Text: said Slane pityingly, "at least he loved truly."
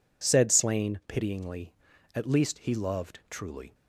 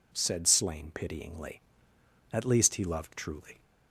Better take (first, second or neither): neither